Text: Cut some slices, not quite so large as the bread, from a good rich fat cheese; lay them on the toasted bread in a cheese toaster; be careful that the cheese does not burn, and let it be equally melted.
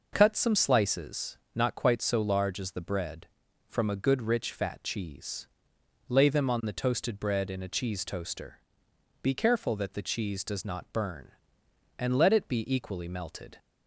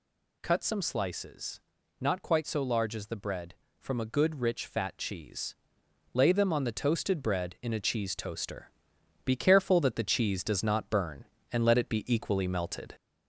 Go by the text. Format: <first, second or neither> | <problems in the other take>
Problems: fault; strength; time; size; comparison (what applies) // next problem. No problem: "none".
first | gets louder; slight; throughout; 2.5 dB